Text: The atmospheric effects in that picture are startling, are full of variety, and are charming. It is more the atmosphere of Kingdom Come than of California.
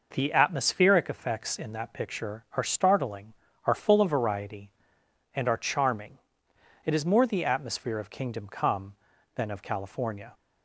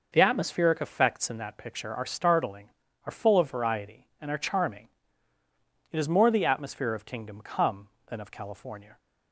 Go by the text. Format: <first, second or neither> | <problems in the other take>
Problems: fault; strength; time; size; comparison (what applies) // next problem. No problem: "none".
neither | none